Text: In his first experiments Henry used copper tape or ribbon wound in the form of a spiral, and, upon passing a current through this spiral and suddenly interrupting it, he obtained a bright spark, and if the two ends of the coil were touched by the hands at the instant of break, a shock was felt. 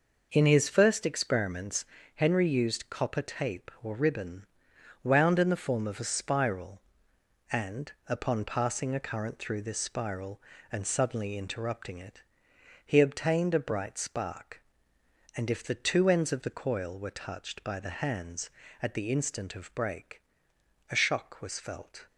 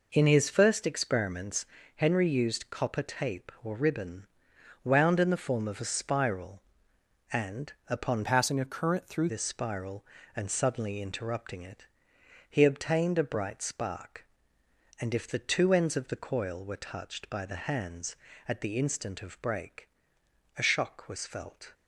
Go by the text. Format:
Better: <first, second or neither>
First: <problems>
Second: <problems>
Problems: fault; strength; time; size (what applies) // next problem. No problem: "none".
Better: first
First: pauses between "experiments" and "Henry"; slight; at 1.8 s; 0.30 s long // pauses between "ribbon" and "wound"; noticeable; at 4.4 s; 0.56 s long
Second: pauses between "experiments" and "Henry"; slight; at 1.6 s; 0.30 s long // pauses between "ribbon" and "wound"; noticeable; at 4.2 s; 0.56 s long // changes voice from "passing" to "through"; from 8.2 to 9.2 s; 1.0 s long